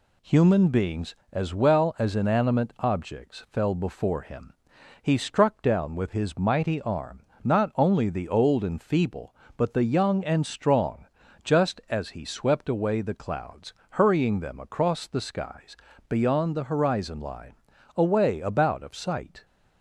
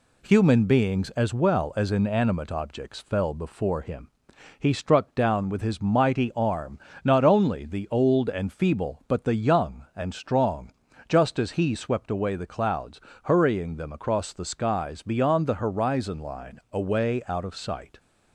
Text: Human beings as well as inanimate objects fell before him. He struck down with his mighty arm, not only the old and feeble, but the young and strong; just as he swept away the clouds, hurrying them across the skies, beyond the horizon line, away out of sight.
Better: second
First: says "about" for "out"; at 18.4 s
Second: none

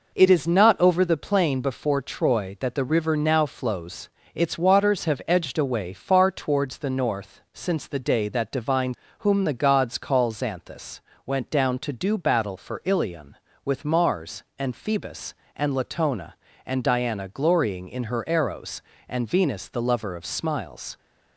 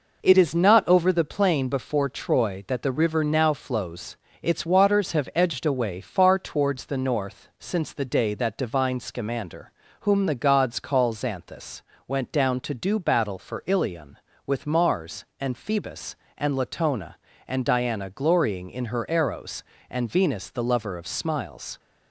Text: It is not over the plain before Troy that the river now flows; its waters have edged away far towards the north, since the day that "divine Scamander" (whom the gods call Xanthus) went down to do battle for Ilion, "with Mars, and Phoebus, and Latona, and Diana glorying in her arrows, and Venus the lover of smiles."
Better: second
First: skips "Scamander"; at 9.0 s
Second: none

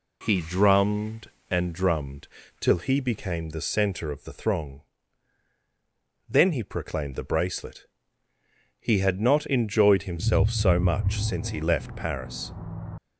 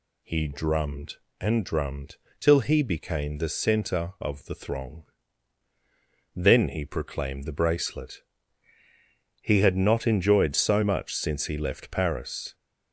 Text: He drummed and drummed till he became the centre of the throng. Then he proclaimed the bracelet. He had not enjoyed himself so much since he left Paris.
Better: first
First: pauses between "drummed" and "till"; slight; at 2.2 s; 0.32 s long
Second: pauses between "drummed" and "till"; slight; at 2.1 s; 0.24 s long // skips "himself"; at 10.5 s

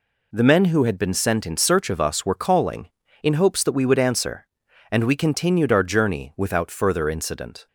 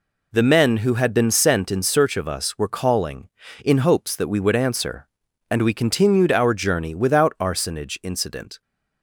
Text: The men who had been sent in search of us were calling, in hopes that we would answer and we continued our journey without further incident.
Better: first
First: none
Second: says "arsonage" for "further"; at 7.3 s

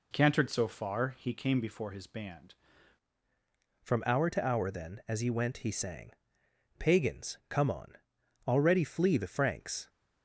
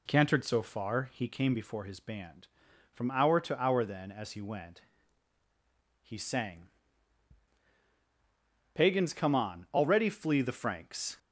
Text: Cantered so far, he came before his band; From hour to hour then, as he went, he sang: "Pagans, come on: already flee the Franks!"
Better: second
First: changes voice at "From"; from 3.8 s on; 6.0 s long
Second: none

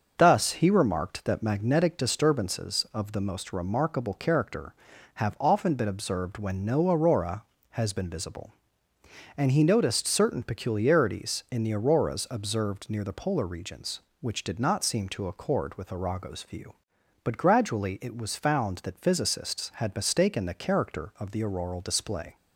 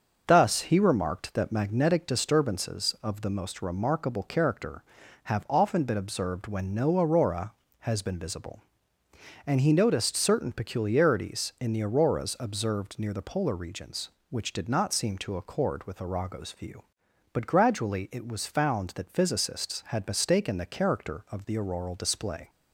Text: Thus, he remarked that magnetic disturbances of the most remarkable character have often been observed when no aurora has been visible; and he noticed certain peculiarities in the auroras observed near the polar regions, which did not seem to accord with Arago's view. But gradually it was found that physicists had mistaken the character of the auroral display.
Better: neither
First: starts louder than the rest; until 1.1 s; 6.5 dB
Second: starts louder than the rest; until 1.2 s; 6.5 dB

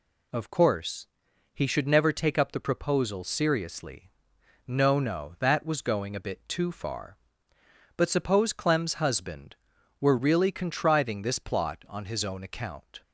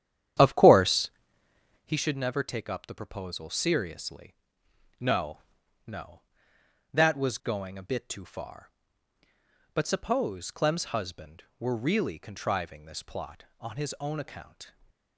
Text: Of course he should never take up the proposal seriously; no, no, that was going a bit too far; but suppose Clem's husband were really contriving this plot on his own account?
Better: first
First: pauses between "course" and "he"; noticeable; at 1.0 s; 0.48 s long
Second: starts louder than the rest; strong; until 1.9 s; 10 dB // pauses between "course" and "he"; noticeable; at 1.0 s; 0.74 s long // stays silent after the last word; slight; from 14.6 s on; 0.5 s long

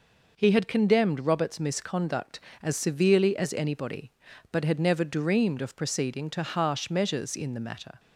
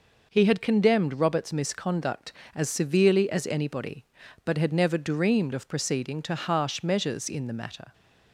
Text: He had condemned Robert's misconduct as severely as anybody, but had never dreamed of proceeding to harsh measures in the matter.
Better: neither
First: none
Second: none

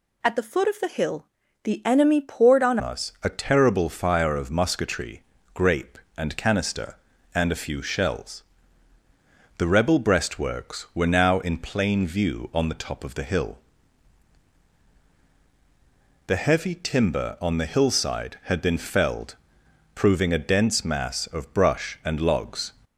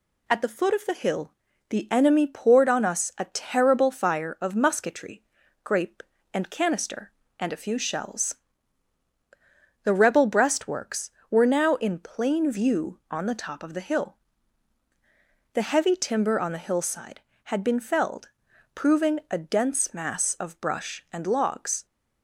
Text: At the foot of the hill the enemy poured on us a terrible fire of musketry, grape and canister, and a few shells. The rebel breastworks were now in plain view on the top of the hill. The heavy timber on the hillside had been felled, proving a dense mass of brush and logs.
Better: second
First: pauses between "hill" and "the"; slight; at 1.2 s; 0.36 s long // changes voice at "us"; from 2.8 s on; 19.9 s long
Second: pauses between "hill" and "the"; slight; at 1.3 s; 0.36 s long

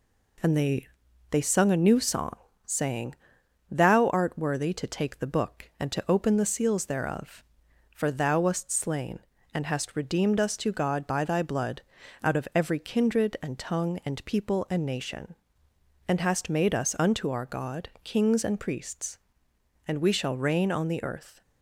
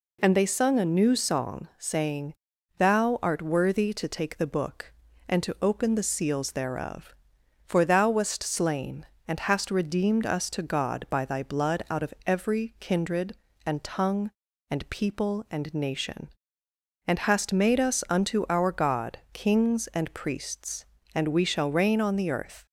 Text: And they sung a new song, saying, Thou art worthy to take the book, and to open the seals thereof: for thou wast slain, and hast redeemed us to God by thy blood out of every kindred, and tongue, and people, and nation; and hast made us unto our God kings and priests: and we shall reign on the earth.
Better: second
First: says "they" twice; at 1.3 s // pauses between "blood" and "out"; at 11.8 s; 0.42 s long // pauses between "God" and "kings"; slight; at 17.8 s; 0.16 s long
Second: none

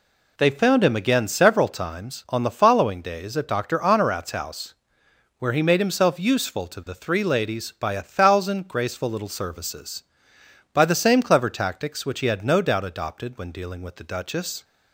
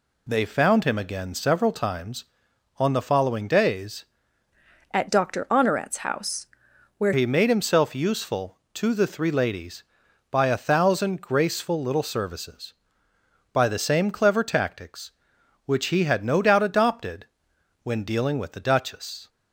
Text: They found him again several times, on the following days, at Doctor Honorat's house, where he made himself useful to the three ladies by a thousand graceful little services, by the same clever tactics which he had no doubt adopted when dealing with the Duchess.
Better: first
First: none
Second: changes voice from "at" to "where"; from 4.9 to 7.1 s; 2.2 s long // pauses between "adopted" and "when"; noticeable; at 17.2 s; 0.56 s long

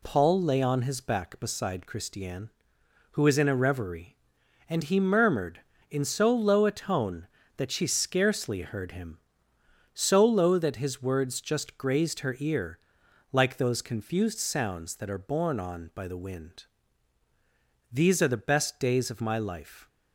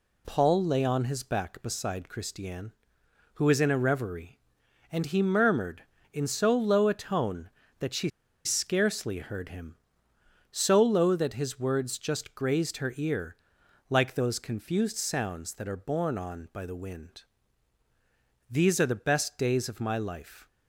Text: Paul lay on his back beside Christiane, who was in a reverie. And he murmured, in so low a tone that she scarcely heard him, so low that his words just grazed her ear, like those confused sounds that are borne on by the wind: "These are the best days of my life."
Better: first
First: none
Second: pauses between "she" and "scarcely"; slight; at 8.0 s; 0.35 s long

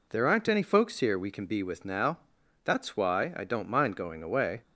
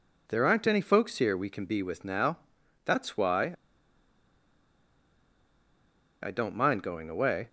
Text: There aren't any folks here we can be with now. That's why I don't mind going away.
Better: first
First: none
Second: pauses between "why" and "I"; strong; at 3.5 s; 2.6 s long

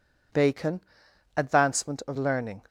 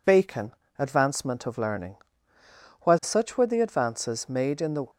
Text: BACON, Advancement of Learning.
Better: first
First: none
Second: goes on to say "While such were the advances made in the"; strong; from 2.8 s on; 2.0 s long

